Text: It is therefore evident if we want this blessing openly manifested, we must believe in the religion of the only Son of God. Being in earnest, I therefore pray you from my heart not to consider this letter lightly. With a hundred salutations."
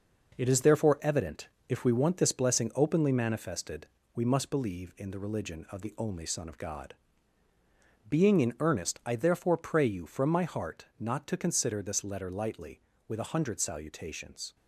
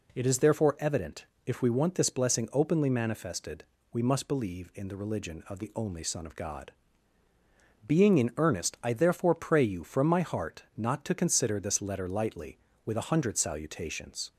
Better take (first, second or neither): second